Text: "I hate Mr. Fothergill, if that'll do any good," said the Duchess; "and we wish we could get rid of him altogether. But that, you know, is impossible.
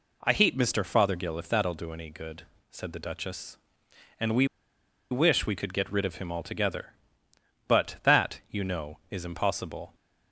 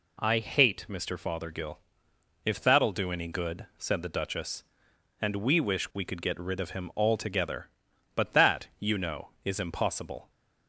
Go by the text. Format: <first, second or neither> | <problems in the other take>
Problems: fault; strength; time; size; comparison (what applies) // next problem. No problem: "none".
second | pauses between "we" and "wish"; noticeable; at 4.4 s; 0.65 s long